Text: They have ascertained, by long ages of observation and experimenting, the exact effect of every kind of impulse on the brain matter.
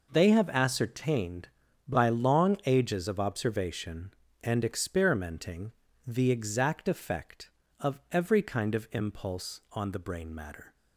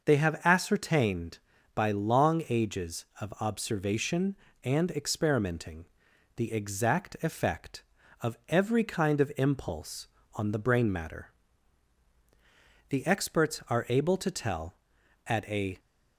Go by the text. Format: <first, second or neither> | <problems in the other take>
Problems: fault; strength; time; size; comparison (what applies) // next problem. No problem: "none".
first | starts louder than the rest; until 1.0 s; 6 dB // goes on to say "The experts are able to tell at a"; strong; from 12.8 s on; 2.9 s long